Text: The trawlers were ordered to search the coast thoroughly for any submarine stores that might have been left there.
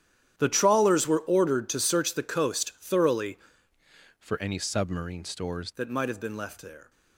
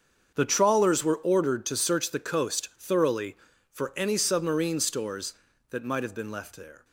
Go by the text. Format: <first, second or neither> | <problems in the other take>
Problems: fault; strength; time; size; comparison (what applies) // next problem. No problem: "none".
second | starts louder than the rest; strong; until 1.3 s; 10.5 dB; also in the second // changes voice from "for" to "stores"; from 4.1 to 5.7 s; 1.6 s long